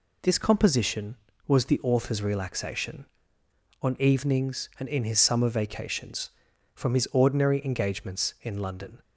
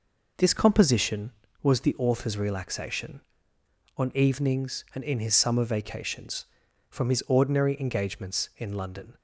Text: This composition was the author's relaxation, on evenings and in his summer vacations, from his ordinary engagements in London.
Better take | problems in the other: first | starts louder than the rest; noticeable; until 1.7 s; 5 dB

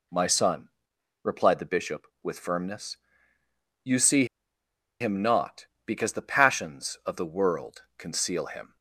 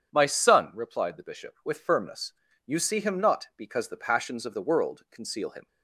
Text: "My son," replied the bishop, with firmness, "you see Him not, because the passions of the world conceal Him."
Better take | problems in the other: second | pauses between "see" and "Him"; noticeable; at 4.2 s; 0.75 s long

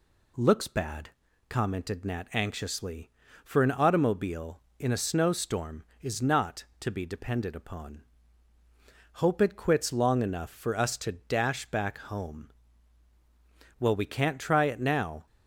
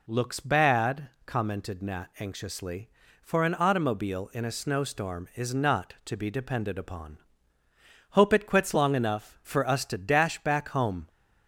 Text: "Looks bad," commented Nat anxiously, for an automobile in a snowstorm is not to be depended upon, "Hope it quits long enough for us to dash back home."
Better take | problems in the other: second | goes on to say "Well we can't try it now"; from 13.7 s on; 1.4 s long

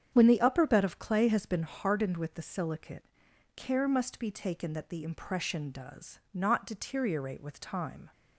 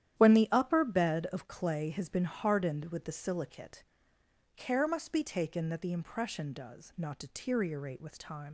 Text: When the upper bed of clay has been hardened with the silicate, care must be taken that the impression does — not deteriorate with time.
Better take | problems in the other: first | starts louder than the rest; strong; until 1.2 s; 11 dB; strong in the first // leaves "time" unfinished; at 8.4 s; 50 ms

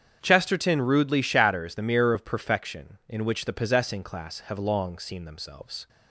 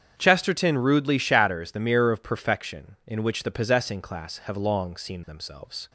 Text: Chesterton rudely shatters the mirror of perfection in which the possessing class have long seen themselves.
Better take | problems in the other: neither | starts louder than the rest; strong; the same in both

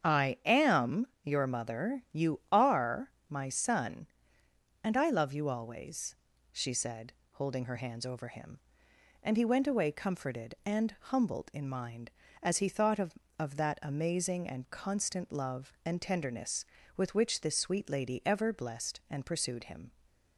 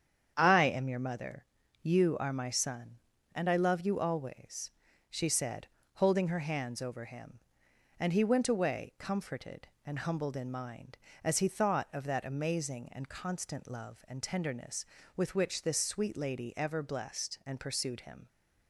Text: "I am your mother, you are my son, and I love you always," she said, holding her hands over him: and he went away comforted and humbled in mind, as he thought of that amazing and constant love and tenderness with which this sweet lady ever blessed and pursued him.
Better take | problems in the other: second | starts louder than the rest; strong; until 1.2 s; 7.5 dB; strong in the second // pauses between "am" and "your"; slight; at 1.0 s; 0.16 s long // pauses between "are" and "my"; slight; at 3.1 s; 0.18 s long // says "of" twice; at 13.3 s

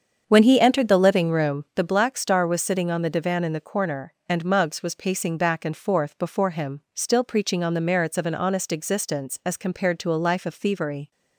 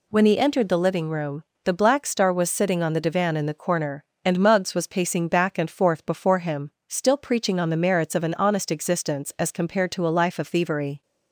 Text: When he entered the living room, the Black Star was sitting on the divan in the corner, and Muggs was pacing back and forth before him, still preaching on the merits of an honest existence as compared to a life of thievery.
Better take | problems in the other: second | starts louder than the rest; strong; until 1.8 s; 7.5 dB

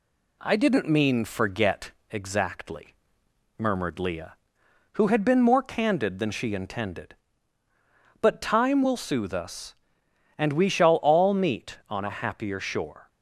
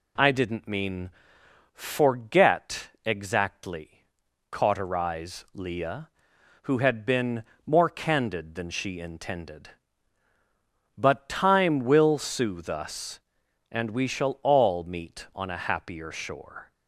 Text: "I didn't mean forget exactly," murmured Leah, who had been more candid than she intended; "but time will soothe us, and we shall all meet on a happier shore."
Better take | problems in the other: first | pauses between "mean" and "forget"; noticeable; at 1.1 s; 0.64 s long // pauses between "forget" and "exactly"; slight; at 2.8 s; 0.16 s long; slight in the first // says "cauterize" for "murmured"; at 4.5 s // pauses between "been" and "more"; slight; at 7.4 s; 0.24 s long

